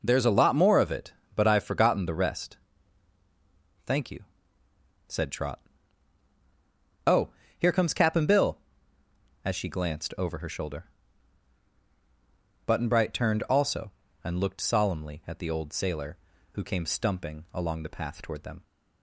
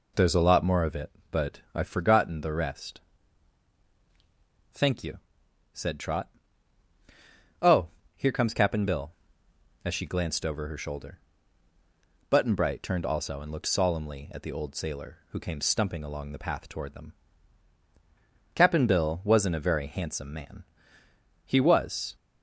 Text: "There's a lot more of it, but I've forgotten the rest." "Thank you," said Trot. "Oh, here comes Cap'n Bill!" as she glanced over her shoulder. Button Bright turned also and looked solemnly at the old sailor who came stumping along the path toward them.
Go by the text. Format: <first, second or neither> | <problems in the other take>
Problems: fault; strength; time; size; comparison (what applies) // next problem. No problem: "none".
first | goes on to say "Cap'n Bill wasn't a very handsome man He was"; strong; from 18.5 s on; 3.6 s long